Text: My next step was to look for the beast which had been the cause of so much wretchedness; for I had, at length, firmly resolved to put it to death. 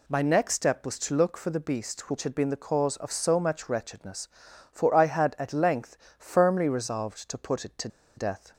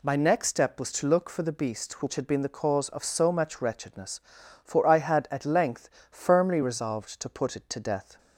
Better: second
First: pauses between "to" and "death"; slight; at 7.8 s; 0.28 s long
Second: none

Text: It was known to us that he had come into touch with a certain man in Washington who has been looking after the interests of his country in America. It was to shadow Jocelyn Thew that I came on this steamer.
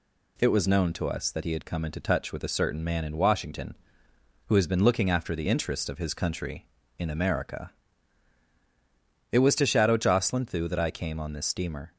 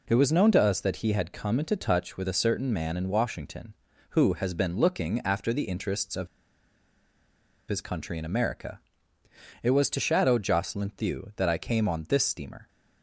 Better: first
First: none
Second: pauses between "of" and "his"; strong; at 6.2 s; 1.4 s long

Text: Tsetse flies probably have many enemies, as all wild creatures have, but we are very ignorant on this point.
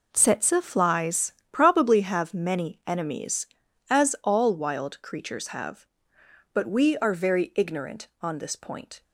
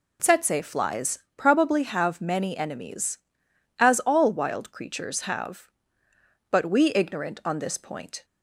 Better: first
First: pauses between "flies" and "probably"; slight; at 1.3 s; 0.22 s long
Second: pauses between "flies" and "probably"; slight; at 1.1 s; 0.18 s long // skips "are very"; at 6.9 s

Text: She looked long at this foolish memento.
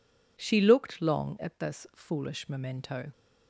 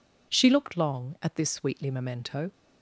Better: first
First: none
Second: says "sweetly" for "foolish"; at 1.4 s

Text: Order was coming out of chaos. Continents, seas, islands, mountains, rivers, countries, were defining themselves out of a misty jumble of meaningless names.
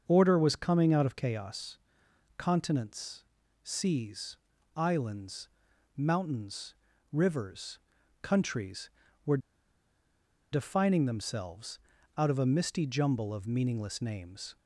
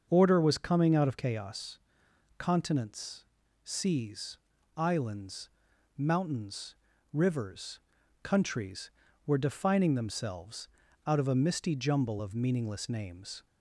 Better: second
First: starts louder than the rest; until 1.0 s; 6.5 dB // pauses between "were" and "defining"; at 9.3 s; 1.1 s long // pauses between "themselves" and "out"; at 11.7 s; 0.40 s long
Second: starts louder than the rest; until 1.1 s; 6.5 dB // pauses between "themselves" and "out"; at 10.6 s; 0.40 s long

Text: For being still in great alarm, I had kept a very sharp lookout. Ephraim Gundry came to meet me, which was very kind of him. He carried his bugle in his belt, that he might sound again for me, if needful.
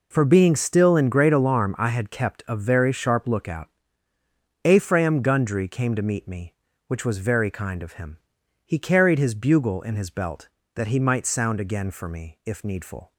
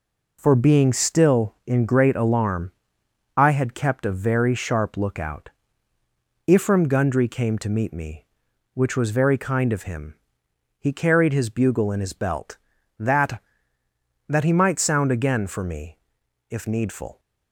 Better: first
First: none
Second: says "that" twice; at 14.2 s

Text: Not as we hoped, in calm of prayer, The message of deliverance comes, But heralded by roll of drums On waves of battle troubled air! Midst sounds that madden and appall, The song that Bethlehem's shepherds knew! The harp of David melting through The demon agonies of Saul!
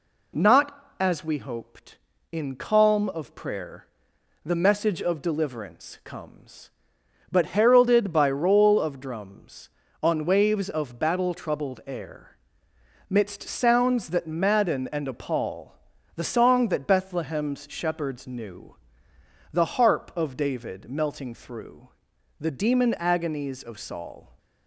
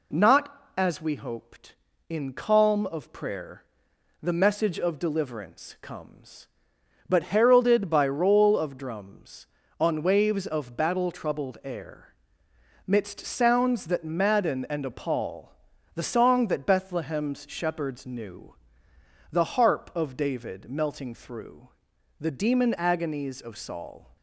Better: neither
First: pauses between "through" and "The"; noticeable; at 21.8 s; 0.50 s long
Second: pauses between "through" and "The"; noticeable; at 21.6 s; 0.50 s long

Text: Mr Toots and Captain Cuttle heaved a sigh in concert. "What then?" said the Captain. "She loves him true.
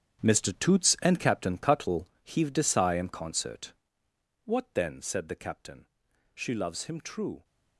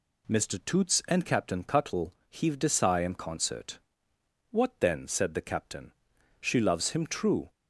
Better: second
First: gets quieter; strong; throughout; 13 dB // pauses between "Cuttle" and "heaved"; slight; at 2.0 s; 0.18 s long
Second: pauses between "Cuttle" and "heaved"; slight; at 2.1 s; 0.18 s long

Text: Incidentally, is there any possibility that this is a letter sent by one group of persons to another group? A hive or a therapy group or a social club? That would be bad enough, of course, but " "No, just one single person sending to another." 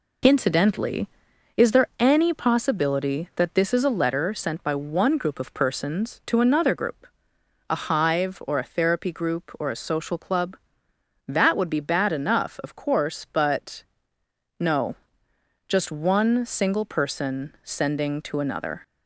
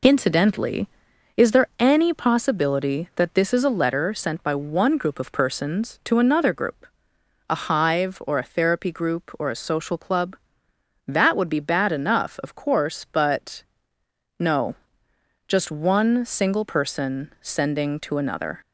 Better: neither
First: none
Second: none

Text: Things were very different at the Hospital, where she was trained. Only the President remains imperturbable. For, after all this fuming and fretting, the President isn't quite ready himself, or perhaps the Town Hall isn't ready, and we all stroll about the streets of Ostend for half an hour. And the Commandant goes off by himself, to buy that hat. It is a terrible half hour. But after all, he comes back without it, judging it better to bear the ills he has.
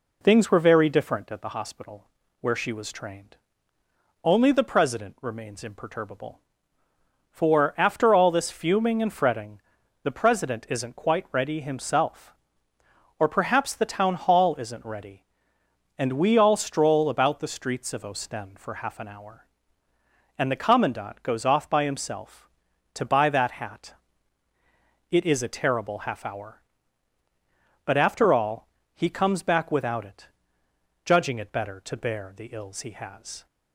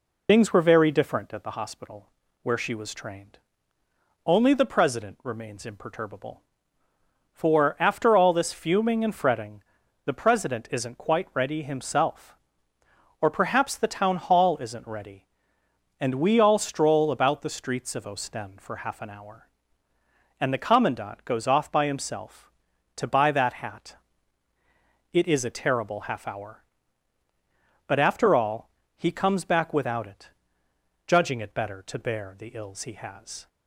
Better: first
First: none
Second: loses the start of "Things"; at 0.2 s; 55 ms

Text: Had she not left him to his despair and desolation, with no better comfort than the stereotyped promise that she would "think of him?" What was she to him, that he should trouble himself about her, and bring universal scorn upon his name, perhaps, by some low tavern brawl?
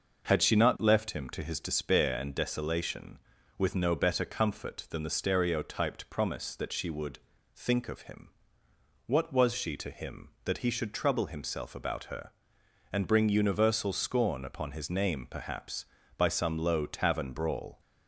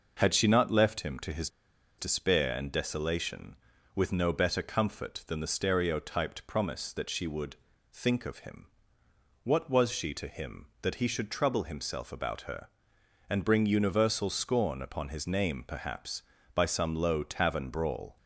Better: first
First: pauses between "would" and "think"; at 7.1 s; 0.38 s long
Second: pauses between "his" and "despair"; noticeable; at 1.4 s; 0.50 s long // pauses between "would" and "think"; at 7.5 s; 0.38 s long

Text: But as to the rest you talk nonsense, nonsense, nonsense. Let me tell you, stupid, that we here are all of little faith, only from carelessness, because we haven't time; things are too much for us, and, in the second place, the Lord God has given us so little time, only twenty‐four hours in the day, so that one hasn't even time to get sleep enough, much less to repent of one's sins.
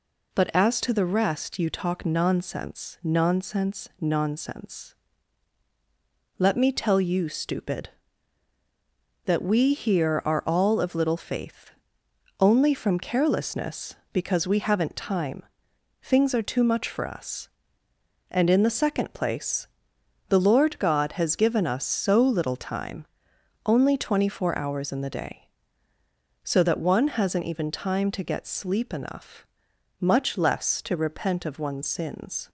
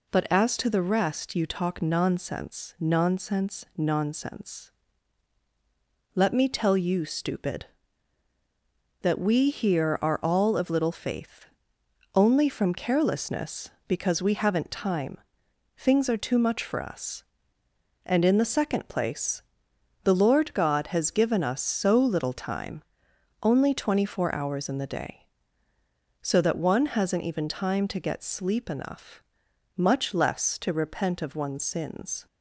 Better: neither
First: none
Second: none

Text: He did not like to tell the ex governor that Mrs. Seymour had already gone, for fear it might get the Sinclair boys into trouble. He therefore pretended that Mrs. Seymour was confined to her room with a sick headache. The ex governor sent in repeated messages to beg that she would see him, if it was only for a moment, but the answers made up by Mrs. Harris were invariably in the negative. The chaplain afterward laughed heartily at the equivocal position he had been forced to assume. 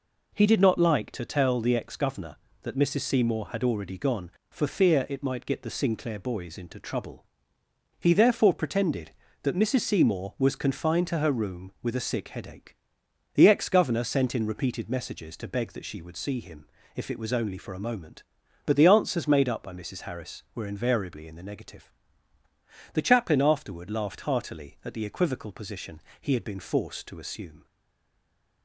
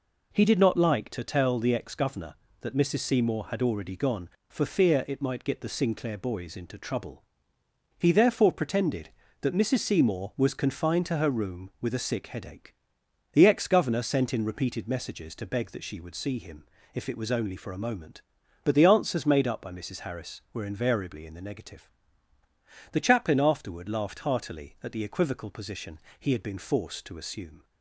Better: second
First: pauses between "position" and "he"; slight; at 25.9 s; 0.20 s long // stays silent after the last word; from 27.6 s on; 1.0 s long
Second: pauses between "position" and "he"; slight; at 25.9 s; 0.20 s long

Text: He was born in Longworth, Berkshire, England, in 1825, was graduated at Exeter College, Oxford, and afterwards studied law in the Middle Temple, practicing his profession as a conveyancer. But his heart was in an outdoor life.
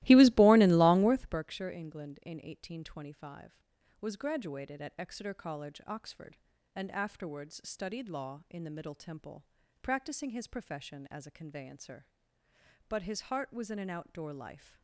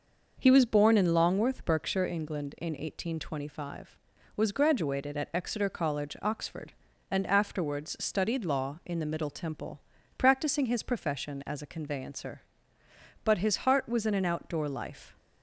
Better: second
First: starts louder than the rest; strong; until 1.4 s; 17.5 dB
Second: none

